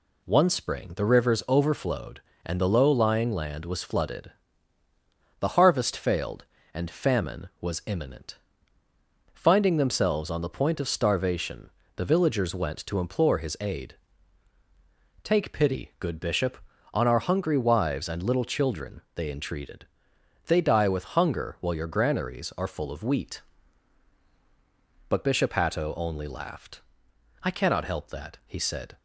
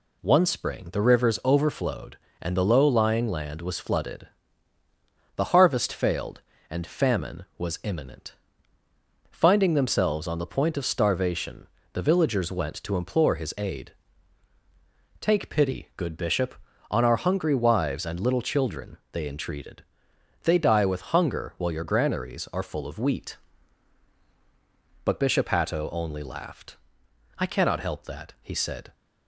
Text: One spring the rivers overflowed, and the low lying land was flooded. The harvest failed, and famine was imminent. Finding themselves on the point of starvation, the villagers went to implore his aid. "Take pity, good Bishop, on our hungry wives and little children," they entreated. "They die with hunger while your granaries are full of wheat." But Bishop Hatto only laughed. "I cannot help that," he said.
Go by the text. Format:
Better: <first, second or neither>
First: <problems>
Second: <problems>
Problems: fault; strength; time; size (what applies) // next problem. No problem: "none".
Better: neither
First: none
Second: none